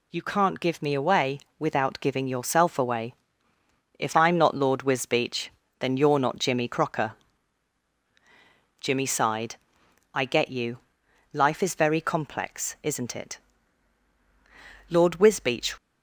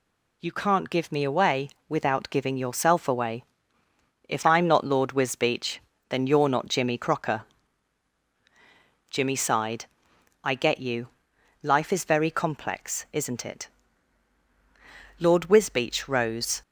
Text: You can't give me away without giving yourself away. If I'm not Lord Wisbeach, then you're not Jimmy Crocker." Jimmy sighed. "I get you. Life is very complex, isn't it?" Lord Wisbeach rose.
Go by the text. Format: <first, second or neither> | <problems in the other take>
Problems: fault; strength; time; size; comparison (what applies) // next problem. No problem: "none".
second | pauses between "away" and "without"; slight; at 1.3 s; 0.18 s long; slight in the second // stops before "rose"; at 15.7 s